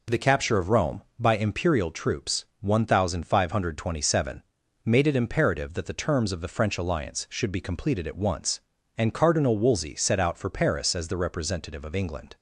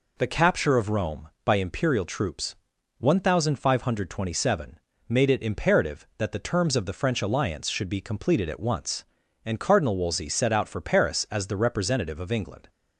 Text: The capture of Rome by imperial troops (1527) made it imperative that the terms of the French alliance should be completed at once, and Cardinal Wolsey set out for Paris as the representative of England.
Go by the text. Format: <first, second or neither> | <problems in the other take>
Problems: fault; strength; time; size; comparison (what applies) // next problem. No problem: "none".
neither | none